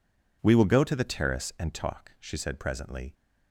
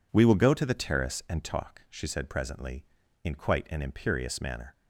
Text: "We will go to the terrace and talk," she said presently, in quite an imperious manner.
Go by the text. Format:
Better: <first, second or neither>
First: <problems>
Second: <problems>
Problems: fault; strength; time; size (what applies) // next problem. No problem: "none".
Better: second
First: stops before "in quite an imperious manner"; at 3.1 s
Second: none